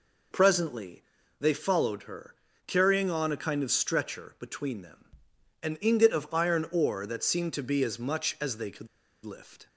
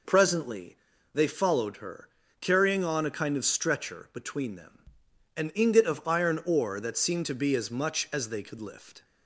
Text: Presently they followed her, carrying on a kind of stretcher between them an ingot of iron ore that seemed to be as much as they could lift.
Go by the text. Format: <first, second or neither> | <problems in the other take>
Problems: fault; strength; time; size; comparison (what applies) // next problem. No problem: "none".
second | pauses between "Presently" and "they"; at 1.0 s; 0.38 s long; also in the second // pauses between "them" and "an"; noticeable; at 5.0 s; 0.58 s long; noticeable in the second // pauses between "could" and "lift"; at 8.8 s; 0.38 s long